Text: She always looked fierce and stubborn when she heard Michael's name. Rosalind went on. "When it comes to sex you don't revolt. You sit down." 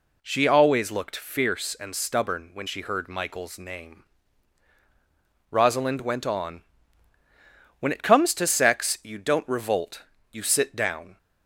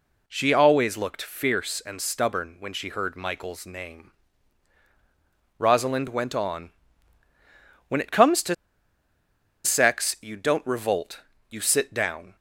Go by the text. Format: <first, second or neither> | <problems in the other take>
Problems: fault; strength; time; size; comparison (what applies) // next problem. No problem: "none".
first | pauses between "to" and "sex"; at 8.5 s; 1.1 s long